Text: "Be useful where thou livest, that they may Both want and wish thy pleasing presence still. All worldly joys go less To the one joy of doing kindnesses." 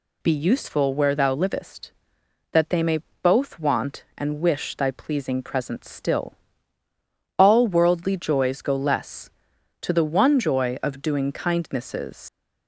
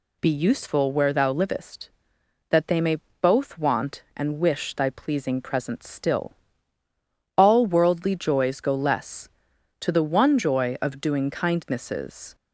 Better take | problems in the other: second | pauses between "may" and "Both"; slight; at 2.9 s; 0.24 s long; slight in the second // leaves "kindnesses" unfinished; at 12.2 s; 90 ms

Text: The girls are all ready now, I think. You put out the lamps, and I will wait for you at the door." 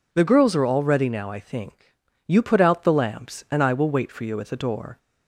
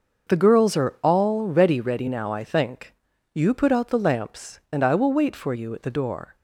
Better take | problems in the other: first | starts louder than the rest; noticeable; until 1.3 s; 6 dB // says "ready" twice; at 1.7 s

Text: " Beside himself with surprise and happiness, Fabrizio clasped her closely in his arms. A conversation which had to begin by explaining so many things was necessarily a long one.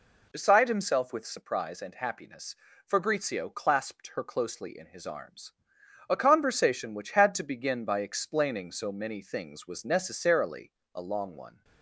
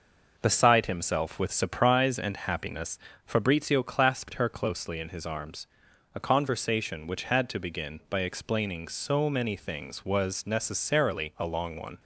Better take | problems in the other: second | changes voice at "Beside"; from 0.3 s on; 11.3 s long // pauses between "necessarily" and "a"; slight; at 10.7 s; 0.22 s long

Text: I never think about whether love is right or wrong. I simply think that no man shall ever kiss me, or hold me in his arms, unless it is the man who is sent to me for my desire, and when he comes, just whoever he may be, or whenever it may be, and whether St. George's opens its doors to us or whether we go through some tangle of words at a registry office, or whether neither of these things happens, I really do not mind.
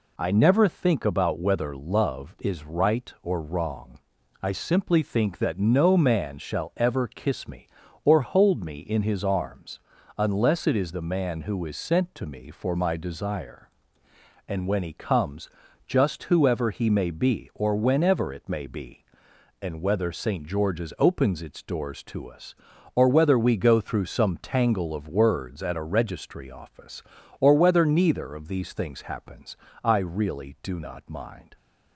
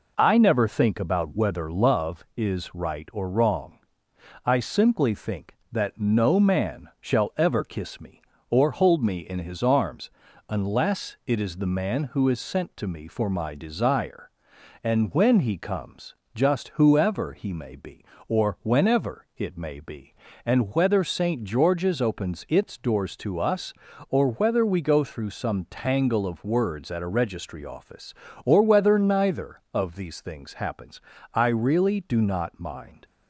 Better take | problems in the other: neither | none

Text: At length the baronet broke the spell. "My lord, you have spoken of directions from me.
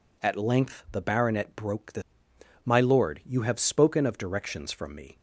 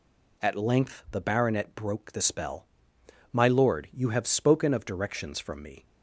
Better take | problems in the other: second | skips "spell"; at 2.3 s

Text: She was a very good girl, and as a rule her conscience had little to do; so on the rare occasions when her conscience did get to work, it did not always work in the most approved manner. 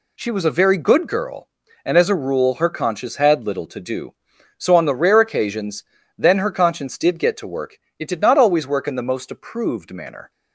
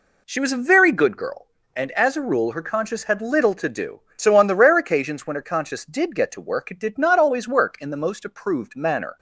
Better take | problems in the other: second | says "then" for "when"; at 6.1 s

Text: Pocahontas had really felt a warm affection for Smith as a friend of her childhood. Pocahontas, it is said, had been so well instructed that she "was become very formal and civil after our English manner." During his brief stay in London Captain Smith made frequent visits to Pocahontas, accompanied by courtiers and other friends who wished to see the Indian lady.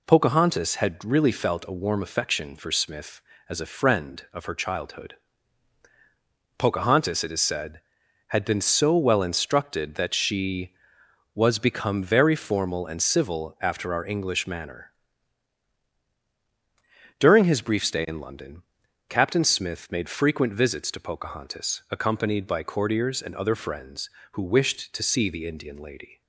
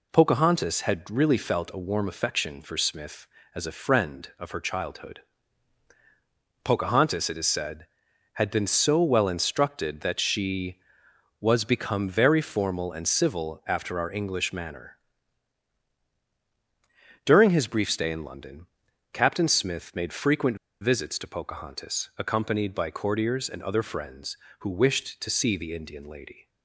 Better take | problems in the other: first | pauses between "London" and "Captain"; noticeable; at 18.6 s; 0.46 s long; noticeable in the first // pauses between "frequent" and "visits"; slight; at 20.5 s; 0.25 s long

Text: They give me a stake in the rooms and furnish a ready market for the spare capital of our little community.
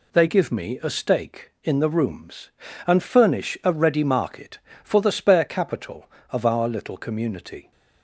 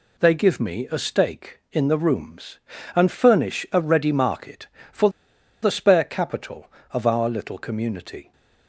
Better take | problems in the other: first | pauses between "for" and "the"; noticeable; at 5.1 s; 0.51 s long

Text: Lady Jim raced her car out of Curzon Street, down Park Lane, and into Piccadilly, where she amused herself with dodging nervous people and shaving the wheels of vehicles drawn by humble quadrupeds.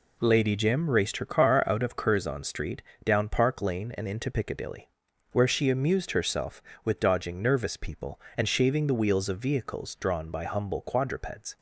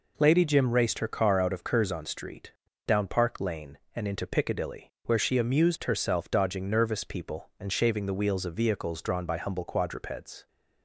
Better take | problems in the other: first | skips "with"; at 6.2 s

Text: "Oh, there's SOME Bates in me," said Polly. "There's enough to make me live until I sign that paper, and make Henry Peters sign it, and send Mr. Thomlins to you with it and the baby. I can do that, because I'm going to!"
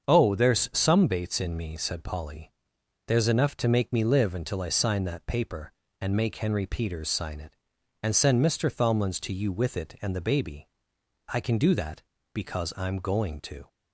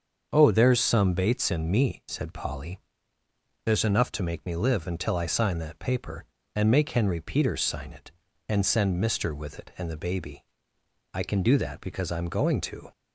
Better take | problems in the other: first | starts louder than the rest; until 1.3 s; 7 dB; also in the first // skips "Thomlins to you"; at 9.3 s

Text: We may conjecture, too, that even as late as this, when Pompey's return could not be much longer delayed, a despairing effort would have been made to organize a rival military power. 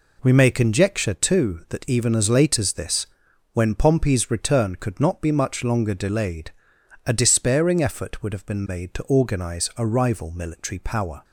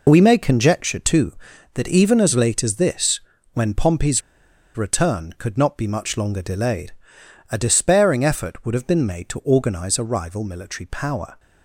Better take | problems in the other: first | pauses between "Pompey's" and "return"; noticeable; at 4.2 s; 0.56 s long

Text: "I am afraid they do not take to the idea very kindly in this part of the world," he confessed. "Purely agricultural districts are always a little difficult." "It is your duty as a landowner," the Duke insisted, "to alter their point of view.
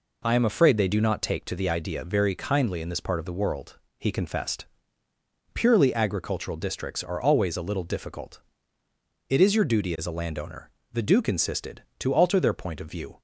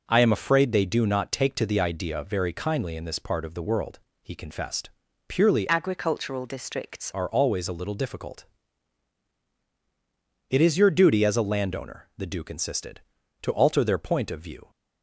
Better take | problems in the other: first | changes voice from "agricultural" to "districts"; from 5.6 to 7.1 s; 1.5 s long

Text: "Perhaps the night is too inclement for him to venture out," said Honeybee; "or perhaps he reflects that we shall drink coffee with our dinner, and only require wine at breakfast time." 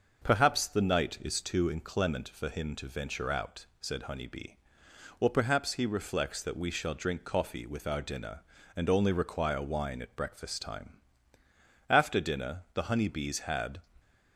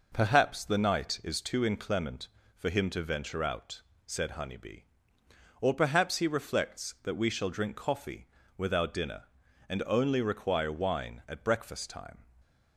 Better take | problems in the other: second | starts louder than the rest; until 1.2 s; 6 dB // goes on to say "After dinner the Honeybees had"; strong; from 11.8 s on; 1.9 s long

